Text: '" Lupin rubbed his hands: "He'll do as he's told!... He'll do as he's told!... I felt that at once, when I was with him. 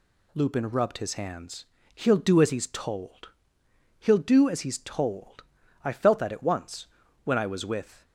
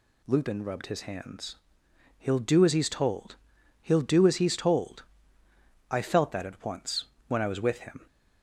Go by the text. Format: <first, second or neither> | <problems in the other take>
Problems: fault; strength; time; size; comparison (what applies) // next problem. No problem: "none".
second | stops before "him"; at 8.0 s